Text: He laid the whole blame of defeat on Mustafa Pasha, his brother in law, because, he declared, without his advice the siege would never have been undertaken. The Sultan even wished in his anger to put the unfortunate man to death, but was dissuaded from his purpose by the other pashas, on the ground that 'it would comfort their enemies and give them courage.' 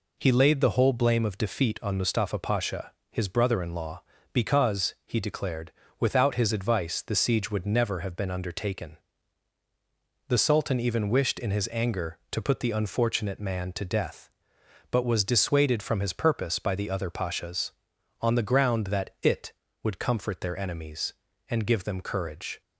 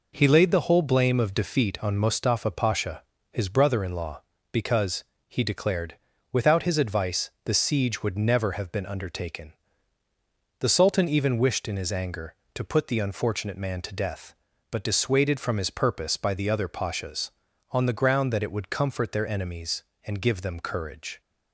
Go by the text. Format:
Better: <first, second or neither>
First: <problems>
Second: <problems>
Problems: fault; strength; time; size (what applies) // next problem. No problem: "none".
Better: first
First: none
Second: skips "was"; at 14.8 s